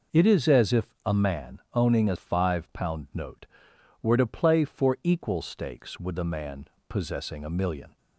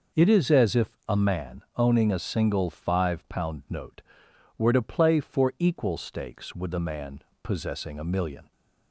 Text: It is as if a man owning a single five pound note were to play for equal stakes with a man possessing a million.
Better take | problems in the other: second | skips "single"; at 2.1 s // pauses between "man" and "possessing"; slight; at 6.6 s; 0.22 s long; slight in the second

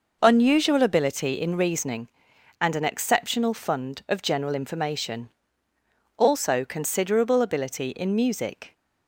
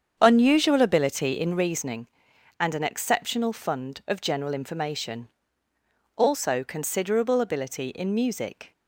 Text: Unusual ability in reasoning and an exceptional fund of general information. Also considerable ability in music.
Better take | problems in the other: first | starts louder than the rest; strong; until 1.7 s; 8 dB

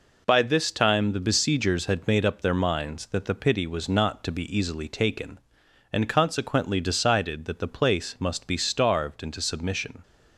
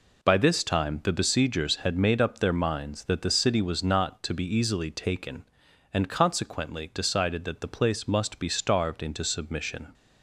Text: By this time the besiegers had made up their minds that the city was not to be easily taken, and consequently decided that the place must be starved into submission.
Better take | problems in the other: second | says "pity" for "city"; at 3.3 s

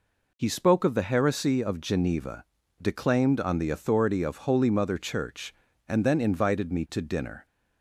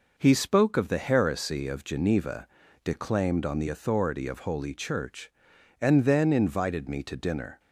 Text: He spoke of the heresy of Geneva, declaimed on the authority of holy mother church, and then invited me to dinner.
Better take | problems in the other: first | skips "mother"; at 4.7 s

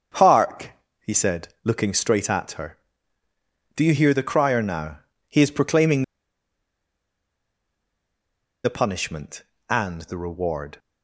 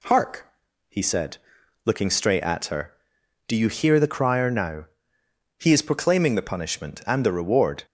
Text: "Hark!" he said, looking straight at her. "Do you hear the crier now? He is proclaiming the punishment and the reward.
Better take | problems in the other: second | starts louder than the rest; until 1.4 s; 7 dB // pauses between "proclaiming" and "the"; strong; at 6.0 s; 2.6 s long

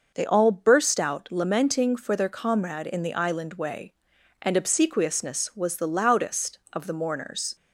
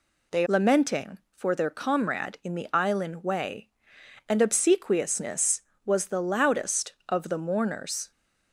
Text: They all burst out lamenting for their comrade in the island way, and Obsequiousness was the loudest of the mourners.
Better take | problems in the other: first | skips "all burst out"; at 0.4 s

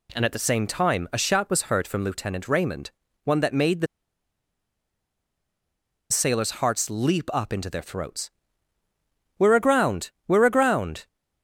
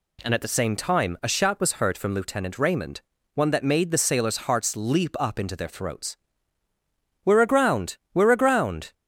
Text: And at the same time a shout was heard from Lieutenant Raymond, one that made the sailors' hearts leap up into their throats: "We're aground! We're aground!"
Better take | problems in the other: second | pauses between "the" and "sailors"; strong; at 3.8 s; 2.2 s long

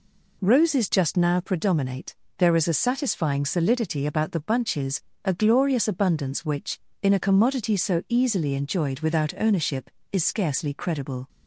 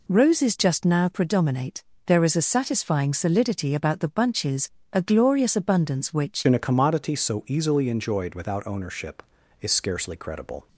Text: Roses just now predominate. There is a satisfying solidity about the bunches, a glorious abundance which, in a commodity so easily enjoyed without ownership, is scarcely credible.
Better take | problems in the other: first | changes voice at "in"; from 6.4 s on; 4.2 s long

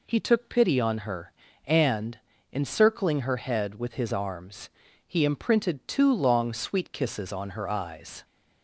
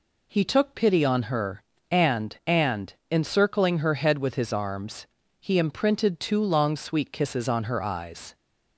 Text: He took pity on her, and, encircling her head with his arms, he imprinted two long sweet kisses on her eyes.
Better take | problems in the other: first | says "and" twice; at 2.4 s

